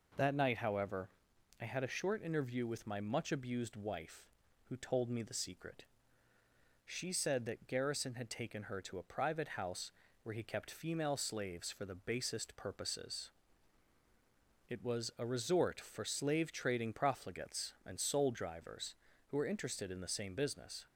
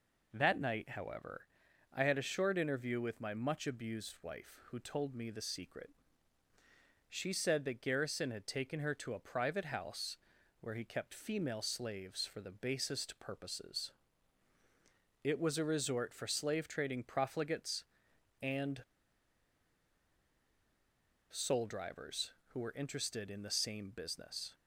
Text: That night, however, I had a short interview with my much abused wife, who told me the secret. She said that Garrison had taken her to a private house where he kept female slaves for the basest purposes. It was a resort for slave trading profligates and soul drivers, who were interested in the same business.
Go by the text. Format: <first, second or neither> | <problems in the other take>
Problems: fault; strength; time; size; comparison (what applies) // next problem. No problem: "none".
first | pauses between "house" and "where"; at 10.1 s; 0.42 s long; slight in the first // pauses between "and" and "soul"; strong; at 18.8 s; 2.4 s long